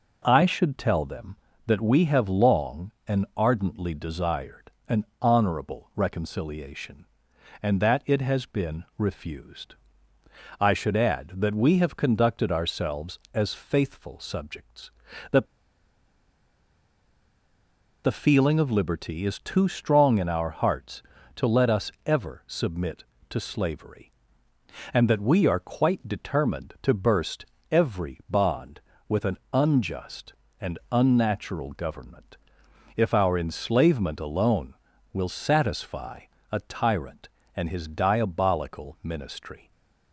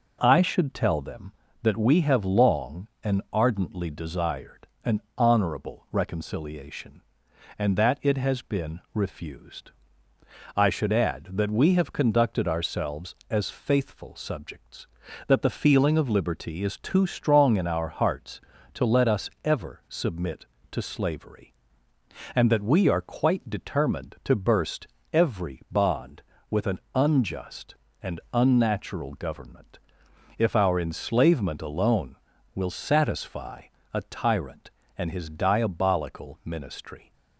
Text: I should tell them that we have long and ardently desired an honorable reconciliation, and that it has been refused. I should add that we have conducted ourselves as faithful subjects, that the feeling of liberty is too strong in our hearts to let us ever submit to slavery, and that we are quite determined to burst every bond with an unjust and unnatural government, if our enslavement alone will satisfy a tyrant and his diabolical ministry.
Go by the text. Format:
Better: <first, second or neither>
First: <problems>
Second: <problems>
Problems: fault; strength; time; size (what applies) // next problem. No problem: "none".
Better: second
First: pauses between "desired" and "an"; slight; at 4.6 s; 0.18 s long // pauses between "an" and "honorable"; slight; at 5.0 s; 0.16 s long // pauses between "that" and "the"; strong; at 15.4 s; 2.5 s long // pauses between "us" and "ever"; slight; at 21.9 s; 0.16 s long // pauses between "burst" and "every"; slight; at 27.4 s; 0.26 s long // pauses between "satisfy" and "a"; slight; at 36.1 s; 0.32 s long // stays silent after the last word; slight; from 39.6 s on; 0.5 s long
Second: pauses between "desired" and "an"; slight; at 4.6 s; 0.18 s long // pauses between "an" and "honorable"; slight; at 5.0 s; 0.16 s long // pauses between "us" and "ever"; slight; at 19.2 s; 0.16 s long // pauses between "burst" and "every"; slight; at 24.8 s; 0.26 s long // pauses between "satisfy" and "a"; slight; at 33.6 s; 0.32 s long